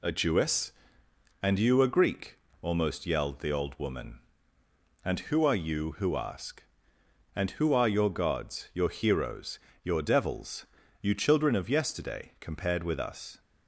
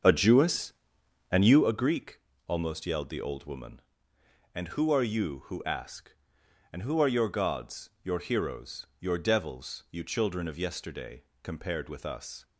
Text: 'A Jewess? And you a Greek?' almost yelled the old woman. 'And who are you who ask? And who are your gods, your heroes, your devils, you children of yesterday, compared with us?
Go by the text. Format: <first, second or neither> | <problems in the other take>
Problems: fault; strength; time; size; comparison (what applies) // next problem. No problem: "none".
first | starts louder than the rest; until 1.7 s; 7 dB